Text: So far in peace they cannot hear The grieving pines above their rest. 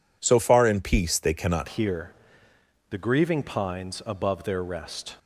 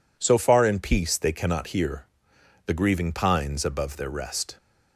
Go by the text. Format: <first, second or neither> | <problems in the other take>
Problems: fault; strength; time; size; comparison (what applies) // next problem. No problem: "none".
second | changes voice at "hear"; from 1.6 s on; 3.5 s long // pauses between "hear" and "The"; noticeable; at 2.1 s; 0.78 s long; noticeable in the second